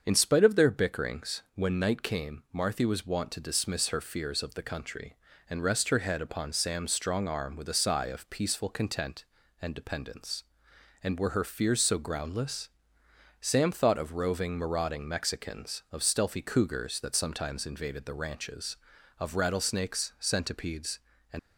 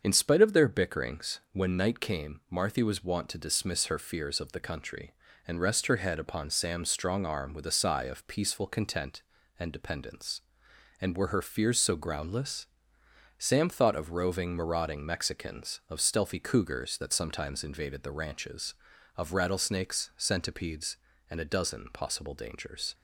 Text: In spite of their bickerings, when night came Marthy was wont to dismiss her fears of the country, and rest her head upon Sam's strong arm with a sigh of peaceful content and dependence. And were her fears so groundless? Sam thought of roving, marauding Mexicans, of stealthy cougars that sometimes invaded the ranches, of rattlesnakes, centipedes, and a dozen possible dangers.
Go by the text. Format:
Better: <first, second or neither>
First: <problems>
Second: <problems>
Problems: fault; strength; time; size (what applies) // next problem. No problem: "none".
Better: second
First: starts louder than the rest; until 1.0 s; 7 dB // stops before "a dozen possible dangers"; at 21.3 s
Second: starts louder than the rest; until 1.0 s; 7 dB